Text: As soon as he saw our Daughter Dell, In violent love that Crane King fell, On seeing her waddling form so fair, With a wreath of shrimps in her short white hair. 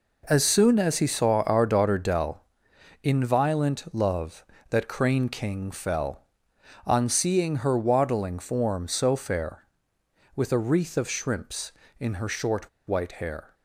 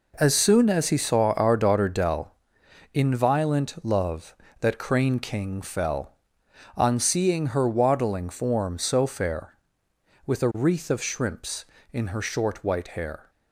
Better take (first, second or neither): second